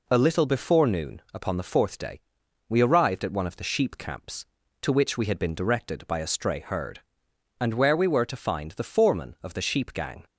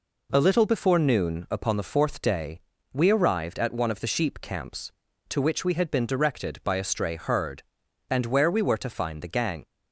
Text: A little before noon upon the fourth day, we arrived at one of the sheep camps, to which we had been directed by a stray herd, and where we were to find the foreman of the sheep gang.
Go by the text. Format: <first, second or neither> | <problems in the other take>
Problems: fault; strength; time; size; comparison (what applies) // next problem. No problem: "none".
first | skips "foreman of the sheep"; at 9.3 s